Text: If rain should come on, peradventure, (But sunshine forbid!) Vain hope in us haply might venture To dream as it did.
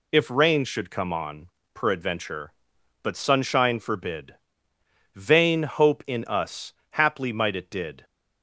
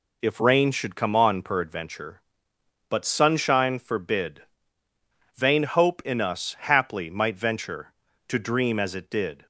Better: second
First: pauses between "us" and "haply"; slight; at 6.7 s; 0.17 s long // skips "venture To dream as"; at 7.5 s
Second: none

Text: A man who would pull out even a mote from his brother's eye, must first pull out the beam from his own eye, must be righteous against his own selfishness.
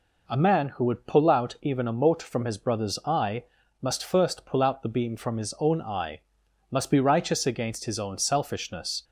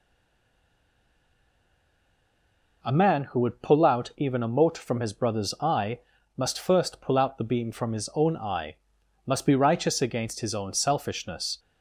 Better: first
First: none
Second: stays silent before the first word; strong; until 2.8 s; 2.8 s long

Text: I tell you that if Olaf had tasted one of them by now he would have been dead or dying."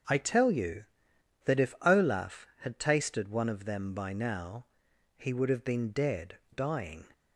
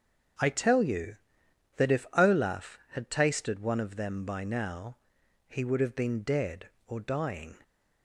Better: second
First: starts louder than the rest; until 1.6 s; 7 dB // pauses between "now" and "he"; noticeable; at 4.6 s; 0.50 s long // skips "or"; at 6.4 s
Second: starts louder than the rest; strong; until 1.9 s; 7.5 dB // pauses between "now" and "he"; noticeable; at 4.9 s; 0.50 s long

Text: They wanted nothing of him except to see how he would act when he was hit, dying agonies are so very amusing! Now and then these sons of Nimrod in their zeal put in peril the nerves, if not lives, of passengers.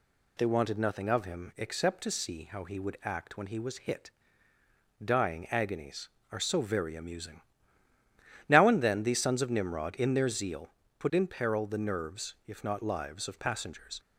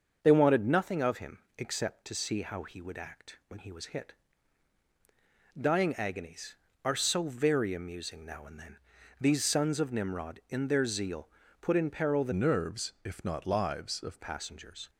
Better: first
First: pauses between "zeal" and "put"; slight; at 10.6 s; 0.30 s long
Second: starts louder than the rest; until 1.2 s; 6.5 dB // pauses between "him" and "except"; slight; at 1.3 s; 0.18 s long // pauses between "then" and "these"; at 8.7 s; 0.42 s long // pauses between "zeal" and "put"; slight; at 11.2 s; 0.32 s long // changes voice from "nerves" to "of"; from 12.3 to 14.1 s; 1.8 s long

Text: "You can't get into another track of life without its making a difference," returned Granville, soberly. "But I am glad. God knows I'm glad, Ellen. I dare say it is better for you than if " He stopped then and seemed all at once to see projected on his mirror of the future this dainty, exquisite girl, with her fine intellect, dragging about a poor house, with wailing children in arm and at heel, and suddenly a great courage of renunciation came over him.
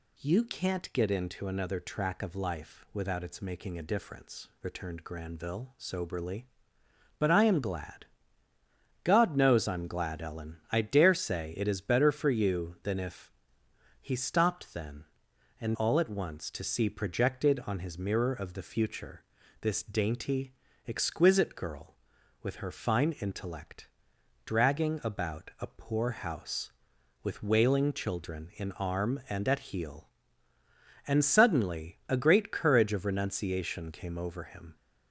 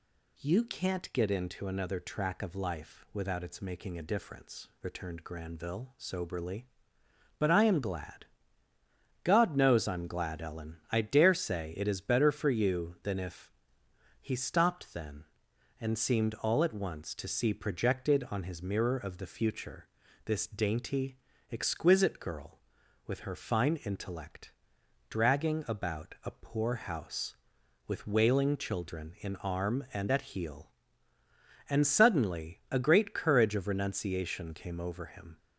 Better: second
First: skips "seemed"; at 15.7 s // pauses between "future" and "this"; at 19.2 s; 0.38 s long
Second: pauses between "future" and "this"; at 19.8 s; 0.38 s long

